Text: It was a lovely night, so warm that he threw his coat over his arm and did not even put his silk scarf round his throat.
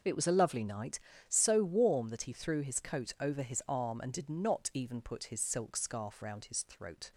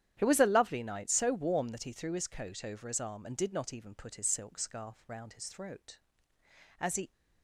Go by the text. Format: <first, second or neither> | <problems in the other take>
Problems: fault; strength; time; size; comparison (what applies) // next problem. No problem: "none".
first | starts louder than the rest; strong; until 1.2 s; 10.5 dB // goes on to say "As he"; slight; from 6.7 s on; 0.32 s long